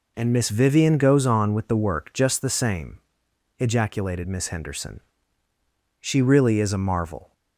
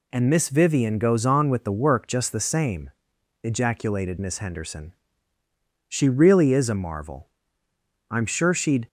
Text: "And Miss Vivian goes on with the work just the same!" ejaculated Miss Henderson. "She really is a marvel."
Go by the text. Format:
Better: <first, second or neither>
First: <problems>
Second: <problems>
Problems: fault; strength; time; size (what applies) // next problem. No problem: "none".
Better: first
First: none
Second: goes on to say "I'm sure she'd"; noticeable; from 8.0 s on; 0.78 s long